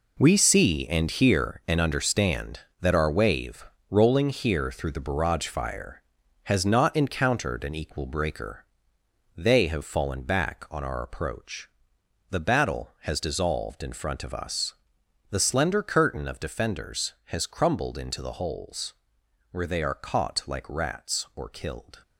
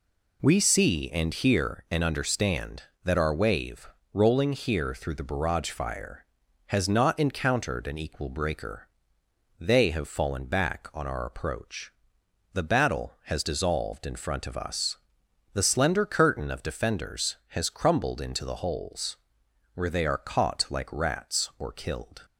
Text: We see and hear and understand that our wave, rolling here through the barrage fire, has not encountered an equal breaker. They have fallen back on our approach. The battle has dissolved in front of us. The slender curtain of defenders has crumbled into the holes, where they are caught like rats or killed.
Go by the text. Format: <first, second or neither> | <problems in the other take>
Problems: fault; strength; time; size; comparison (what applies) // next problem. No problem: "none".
second | gets quieter; strong; throughout; 9.5 dB